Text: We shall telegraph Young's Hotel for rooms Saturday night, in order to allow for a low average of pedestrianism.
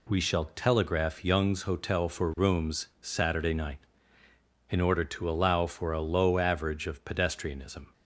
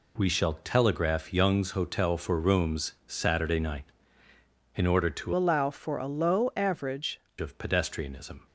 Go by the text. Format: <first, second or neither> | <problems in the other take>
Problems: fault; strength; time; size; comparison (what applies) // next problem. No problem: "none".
first | changes voice from "allow" to "average"; from 5.3 to 7.2 s; 1.9 s long